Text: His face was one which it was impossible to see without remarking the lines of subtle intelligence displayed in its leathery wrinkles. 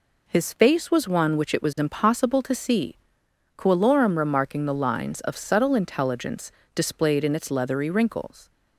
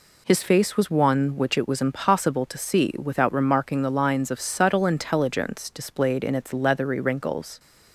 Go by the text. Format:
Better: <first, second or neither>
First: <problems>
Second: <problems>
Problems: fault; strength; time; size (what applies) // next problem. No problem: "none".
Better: second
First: says "coelorum" for "without"; at 3.5 s // pauses between "intelligence" and "displayed"; slight; at 6.5 s; 0.22 s long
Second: none